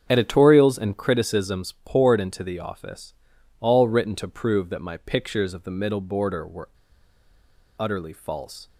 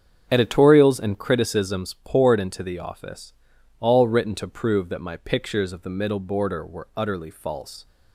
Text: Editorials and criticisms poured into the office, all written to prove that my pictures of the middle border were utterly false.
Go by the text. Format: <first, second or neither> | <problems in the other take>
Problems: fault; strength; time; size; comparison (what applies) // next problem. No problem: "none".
second | starts louder than the rest; strong; until 1.0 s; 7.5 dB; strong in the second // pauses between "were" and "utterly"; at 6.6 s; 1.1 s long